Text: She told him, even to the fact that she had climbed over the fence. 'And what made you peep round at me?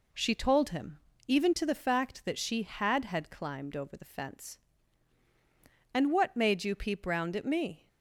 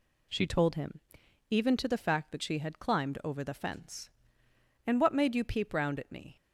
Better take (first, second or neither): second